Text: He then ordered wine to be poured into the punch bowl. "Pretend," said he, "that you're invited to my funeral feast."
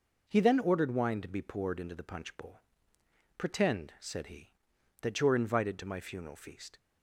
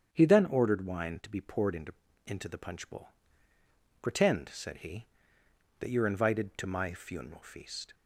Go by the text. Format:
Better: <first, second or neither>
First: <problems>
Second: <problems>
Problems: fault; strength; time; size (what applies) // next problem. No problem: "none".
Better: first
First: none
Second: starts louder than the rest; strong; until 1.1 s; 8.5 dB // says "into" twice; at 2.2 s